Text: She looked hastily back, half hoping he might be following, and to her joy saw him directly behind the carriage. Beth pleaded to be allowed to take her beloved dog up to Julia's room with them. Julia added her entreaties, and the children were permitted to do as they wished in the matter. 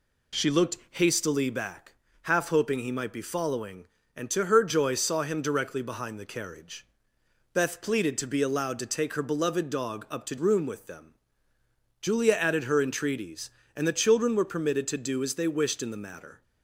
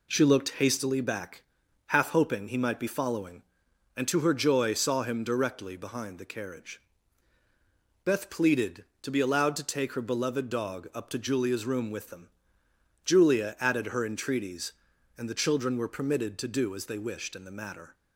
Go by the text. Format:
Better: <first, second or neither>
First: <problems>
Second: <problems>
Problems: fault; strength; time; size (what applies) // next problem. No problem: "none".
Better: second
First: skips "Julia's"; at 10.3 s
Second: none